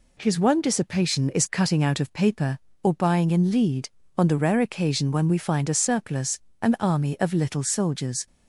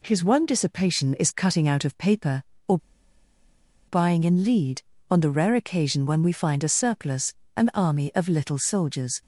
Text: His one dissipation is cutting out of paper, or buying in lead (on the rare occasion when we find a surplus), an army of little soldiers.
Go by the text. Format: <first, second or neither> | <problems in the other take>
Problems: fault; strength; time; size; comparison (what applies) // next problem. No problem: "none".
first | pauses between "or" and "buying"; at 2.7 s; 1.1 s long